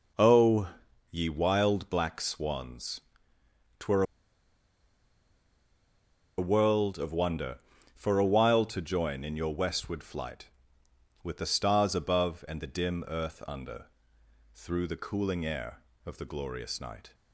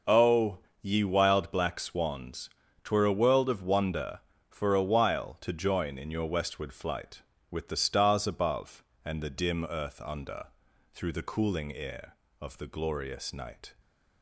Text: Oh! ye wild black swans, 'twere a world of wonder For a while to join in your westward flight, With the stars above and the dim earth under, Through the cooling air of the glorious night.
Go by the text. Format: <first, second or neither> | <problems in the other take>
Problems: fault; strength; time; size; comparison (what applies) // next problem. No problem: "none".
second | pauses between "twere" and "a"; strong; at 4.0 s; 2.3 s long